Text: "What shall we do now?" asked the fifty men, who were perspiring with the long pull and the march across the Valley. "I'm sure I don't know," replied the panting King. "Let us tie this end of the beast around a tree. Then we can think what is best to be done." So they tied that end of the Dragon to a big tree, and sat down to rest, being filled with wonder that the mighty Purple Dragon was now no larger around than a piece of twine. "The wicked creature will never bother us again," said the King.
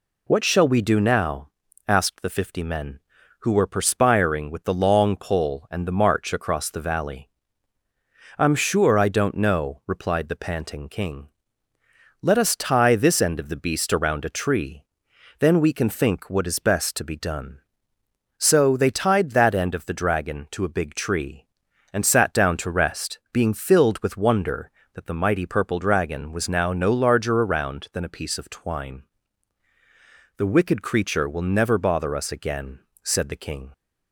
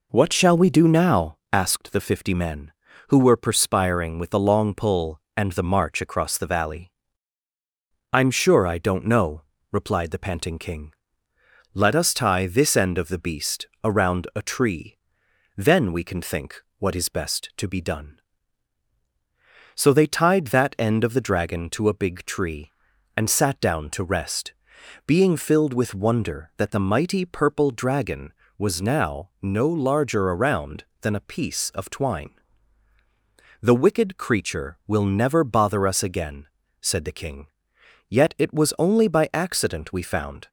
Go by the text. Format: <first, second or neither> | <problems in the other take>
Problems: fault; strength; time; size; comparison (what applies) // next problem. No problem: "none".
first | pauses between "beast" and "around"; slight; at 13.6 s; 0.18 s long // pauses between "think" and "what"; slight; at 16.6 s; 0.18 s long // goes on to say "Yet it was only by accident we found"; strong; from 38.0 s on; 2.4 s long